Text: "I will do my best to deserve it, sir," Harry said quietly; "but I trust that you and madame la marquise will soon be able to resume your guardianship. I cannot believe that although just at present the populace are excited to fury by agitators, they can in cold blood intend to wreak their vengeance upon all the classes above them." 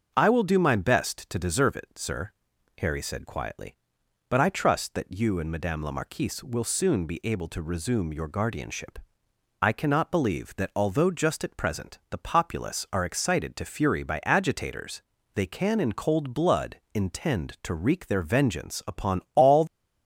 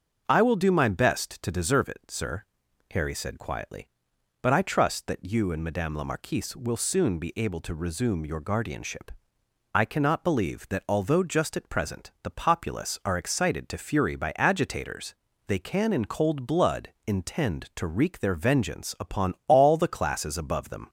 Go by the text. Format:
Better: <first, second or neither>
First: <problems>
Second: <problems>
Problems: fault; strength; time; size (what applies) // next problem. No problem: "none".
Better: second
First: starts louder than the rest; until 1.1 s; 7 dB // stops before "the classes above them"; at 19.6 s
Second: starts louder than the rest; until 1.2 s; 6.5 dB